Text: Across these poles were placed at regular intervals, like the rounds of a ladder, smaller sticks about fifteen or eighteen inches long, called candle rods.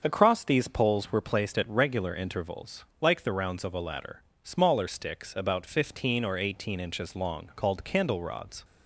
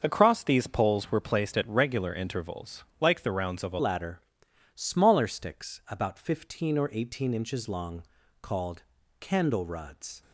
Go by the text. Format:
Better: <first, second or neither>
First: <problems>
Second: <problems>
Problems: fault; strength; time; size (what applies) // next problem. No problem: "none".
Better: first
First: starts louder than the rest; until 1.0 s; 6.5 dB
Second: starts louder than the rest; until 1.0 s; 6.5 dB // changes voice at "ladder"; from 3.7 s on; 6.5 s long // pauses between "called" and "candle"; at 8.8 s; 0.38 s long